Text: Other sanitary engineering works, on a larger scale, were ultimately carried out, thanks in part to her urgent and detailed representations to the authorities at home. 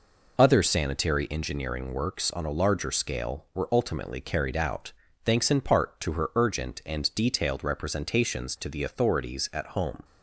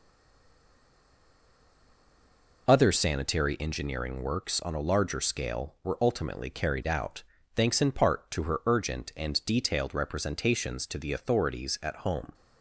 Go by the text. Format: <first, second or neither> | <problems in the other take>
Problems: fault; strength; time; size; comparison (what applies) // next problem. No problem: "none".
first | stays silent before the first word; strong; until 2.6 s; 2.6 s long